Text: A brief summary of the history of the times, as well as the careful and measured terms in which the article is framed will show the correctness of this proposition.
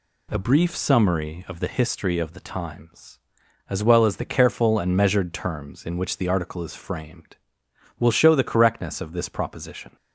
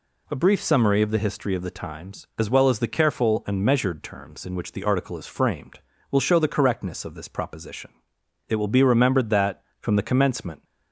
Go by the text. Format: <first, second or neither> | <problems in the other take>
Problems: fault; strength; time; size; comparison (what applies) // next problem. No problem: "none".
first | goes on to say "It will be remembered that from the commencement"; strong; from 8.4 s on; 2.1 s long